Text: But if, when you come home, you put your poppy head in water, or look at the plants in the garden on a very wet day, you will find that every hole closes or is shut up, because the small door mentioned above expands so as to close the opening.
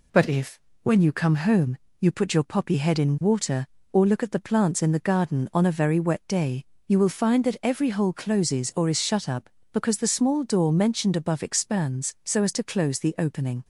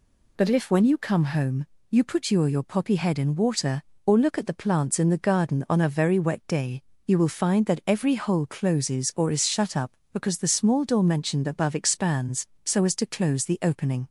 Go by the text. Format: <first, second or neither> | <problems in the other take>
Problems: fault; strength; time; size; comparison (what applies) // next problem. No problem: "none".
first | says "your" twice; at 2.4 s